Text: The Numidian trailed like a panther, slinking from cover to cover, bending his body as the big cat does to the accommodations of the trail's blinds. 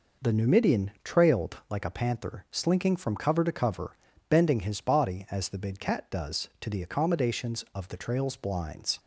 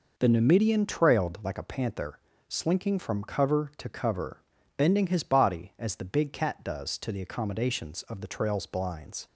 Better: neither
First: none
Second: none

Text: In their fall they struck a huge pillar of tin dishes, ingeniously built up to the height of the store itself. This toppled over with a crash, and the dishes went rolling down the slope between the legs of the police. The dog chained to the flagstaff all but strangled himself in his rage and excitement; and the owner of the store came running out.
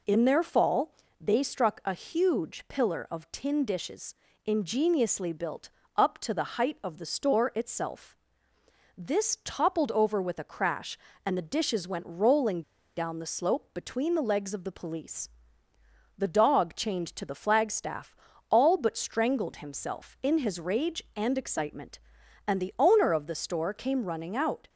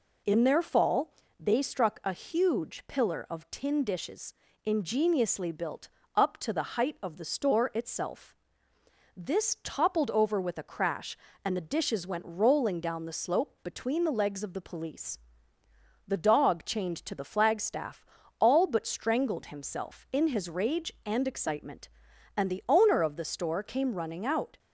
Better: second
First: pauses between "fall" and "they"; slight; at 0.9 s; 0.28 s long // pauses between "built" and "up"; slight; at 5.6 s; 0.28 s long // pauses between "rolling" and "down"; slight; at 12.6 s; 0.34 s long // pauses between "flagstaff" and "all"; slight; at 18.1 s; 0.36 s long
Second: pauses between "fall" and "they"; slight; at 1.1 s; 0.28 s long // pauses between "built" and "up"; slight; at 5.8 s; 0.28 s long // pauses between "flagstaff" and "all"; slight; at 18.0 s; 0.36 s long

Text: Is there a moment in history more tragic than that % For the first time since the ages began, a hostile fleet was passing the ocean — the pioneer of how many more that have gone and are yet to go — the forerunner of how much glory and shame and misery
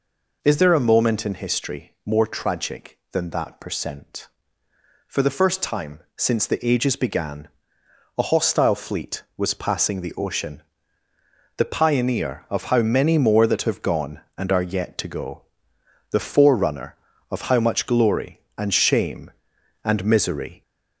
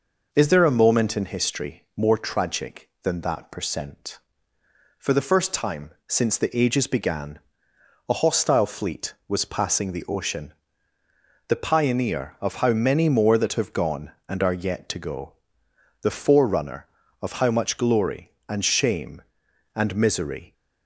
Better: second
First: gets louder; slight; throughout; 3 dB // pauses between "time" and "since"; slight; at 5.9 s; 0.16 s long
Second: pauses between "time" and "since"; slight; at 5.9 s; 0.16 s long

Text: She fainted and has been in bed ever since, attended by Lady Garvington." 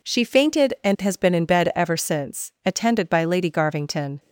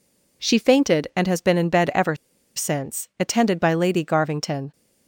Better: first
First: none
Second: pauses between "ever" and "since"; at 2.1 s; 0.41 s long

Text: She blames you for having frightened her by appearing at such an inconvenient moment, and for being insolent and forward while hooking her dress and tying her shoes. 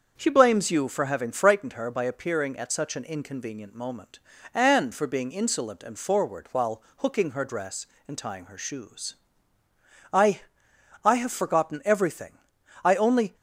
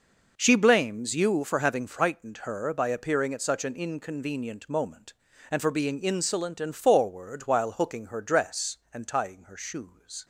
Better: second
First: starts louder than the rest; until 1.1 s; 6.5 dB // pauses between "while" and "hooking"; slight; at 6.8 s; 0.16 s long // goes on to say "I I have forgotten everything I only"; strong; from 10.1 s on; 3.2 s long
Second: none

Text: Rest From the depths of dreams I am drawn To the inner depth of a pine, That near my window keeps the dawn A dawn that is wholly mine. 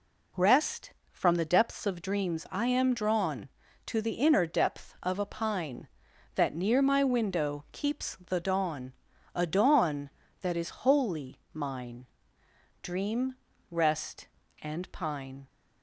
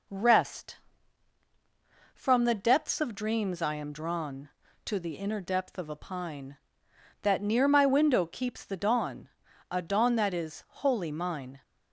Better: second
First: pauses between "dawn" and "A"; at 8.9 s; 0.40 s long // goes on to say "Dream rest and pine"; strong; from 12.8 s on; 2.6 s long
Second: pauses between "dawn" and "A"; at 9.2 s; 0.42 s long

